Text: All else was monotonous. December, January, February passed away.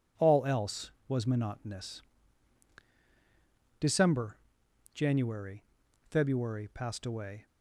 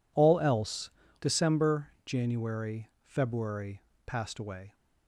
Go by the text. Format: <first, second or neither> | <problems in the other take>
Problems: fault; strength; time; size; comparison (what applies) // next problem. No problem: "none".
first | skips "was monotonous"; at 1.0 s // pauses between "February" and "passed"; slight; at 3.8 s; 0.24 s long